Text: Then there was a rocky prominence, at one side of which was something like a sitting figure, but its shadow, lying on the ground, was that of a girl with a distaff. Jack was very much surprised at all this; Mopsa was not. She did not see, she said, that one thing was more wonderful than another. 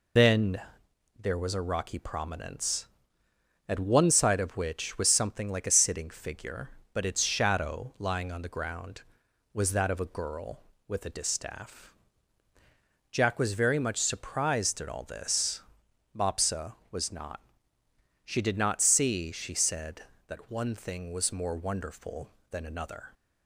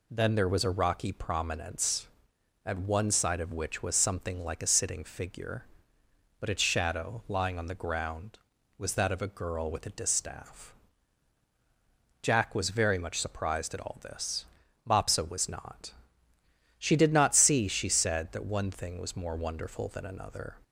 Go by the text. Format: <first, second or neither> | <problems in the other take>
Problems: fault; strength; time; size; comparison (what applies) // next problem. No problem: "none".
second | loses the start of "Then"; at 0.1 s; 125 ms // pauses between "Then" and "there"; noticeable; at 0.6 s; 0.58 s long